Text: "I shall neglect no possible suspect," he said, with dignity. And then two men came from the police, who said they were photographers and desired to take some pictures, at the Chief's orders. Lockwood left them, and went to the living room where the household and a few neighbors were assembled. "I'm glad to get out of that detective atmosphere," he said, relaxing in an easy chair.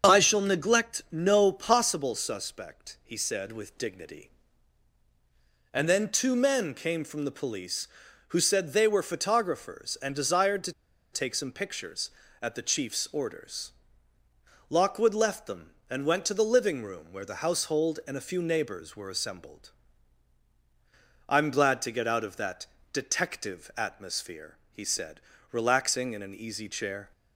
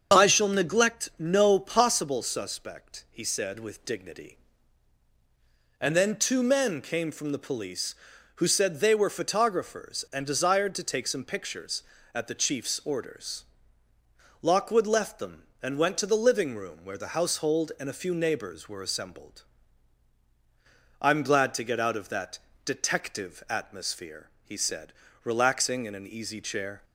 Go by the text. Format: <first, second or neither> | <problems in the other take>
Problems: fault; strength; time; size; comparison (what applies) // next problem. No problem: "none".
second | starts louder than the rest; strong; until 1.1 s; 7 dB; also in the second // pauses between "to" and "take"; at 10.7 s; 0.41 s long // pauses between "that" and "detective"; slight; at 22.6 s; 0.26 s long; slight in the second